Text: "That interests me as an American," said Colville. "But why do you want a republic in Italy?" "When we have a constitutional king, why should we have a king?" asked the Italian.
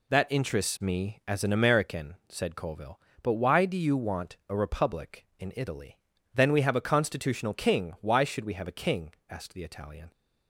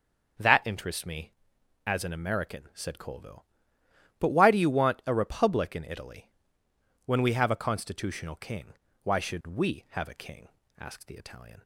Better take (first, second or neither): second